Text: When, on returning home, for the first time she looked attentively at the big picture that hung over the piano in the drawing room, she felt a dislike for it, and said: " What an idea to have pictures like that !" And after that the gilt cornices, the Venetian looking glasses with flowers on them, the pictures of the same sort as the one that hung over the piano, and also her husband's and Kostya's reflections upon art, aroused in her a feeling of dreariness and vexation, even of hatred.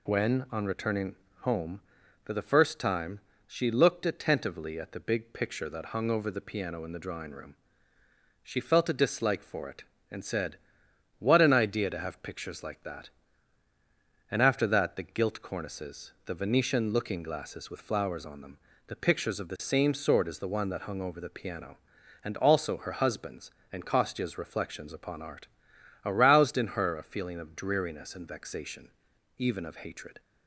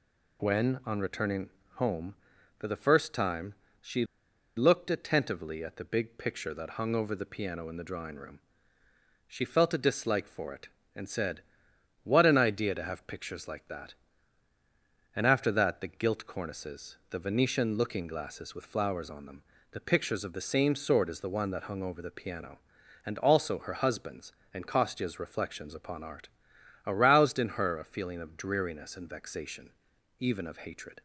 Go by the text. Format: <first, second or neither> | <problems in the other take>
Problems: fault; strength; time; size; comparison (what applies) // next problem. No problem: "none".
first | pauses between "returning" and "home"; slight; at 1.5 s; 0.24 s long; slight in the first // pauses between "time" and "she"; slight; at 3.5 s; 0.26 s long; slight in the first // pauses between "she" and "looked"; noticeable; at 4.0 s; 0.50 s long